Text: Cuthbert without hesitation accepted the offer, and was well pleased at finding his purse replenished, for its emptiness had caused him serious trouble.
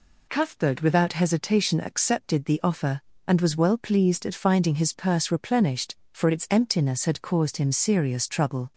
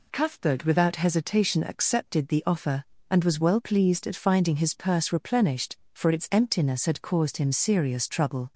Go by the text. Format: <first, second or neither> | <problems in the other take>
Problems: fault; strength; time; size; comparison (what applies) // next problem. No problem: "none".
neither | none